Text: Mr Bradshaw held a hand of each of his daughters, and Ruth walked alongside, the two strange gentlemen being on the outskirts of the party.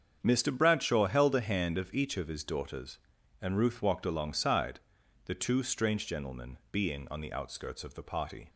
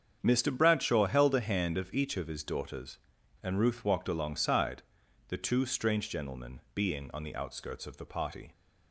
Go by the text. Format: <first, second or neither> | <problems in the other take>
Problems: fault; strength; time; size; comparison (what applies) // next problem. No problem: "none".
neither | starts louder than the rest; strong; the same in both // pauses between "gentlemen" and "being"; slight; the same in both